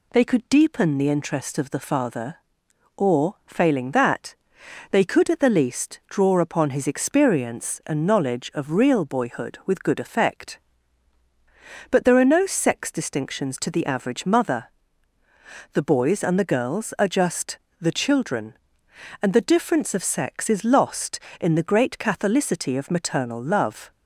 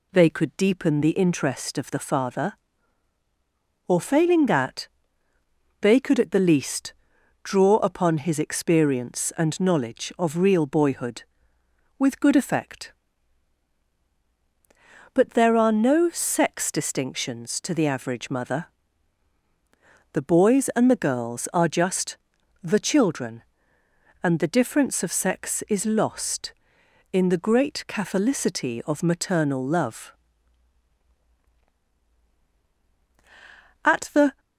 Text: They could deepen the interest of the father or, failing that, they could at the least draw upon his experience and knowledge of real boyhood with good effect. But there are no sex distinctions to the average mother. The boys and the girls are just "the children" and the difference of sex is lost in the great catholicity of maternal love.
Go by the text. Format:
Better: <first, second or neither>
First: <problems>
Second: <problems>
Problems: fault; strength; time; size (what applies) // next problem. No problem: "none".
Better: first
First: pauses between "just" and "the"; slight; at 17.5 s; 0.20 s long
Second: pauses between "least" and "draw"; noticeable; at 6.9 s; 0.48 s long // pauses between "just" and "the"; noticeable; at 22.1 s; 0.46 s long // goes on to say "At the"; from 33.8 s on; 0.56 s long